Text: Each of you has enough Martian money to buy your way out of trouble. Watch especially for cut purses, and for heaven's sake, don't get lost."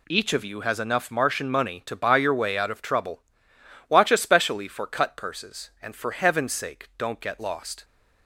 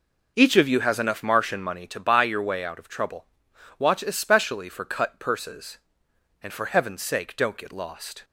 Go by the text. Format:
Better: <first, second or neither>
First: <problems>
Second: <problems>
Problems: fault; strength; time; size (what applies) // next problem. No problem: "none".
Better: first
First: none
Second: starts louder than the rest; noticeable; until 1.8 s; 5.5 dB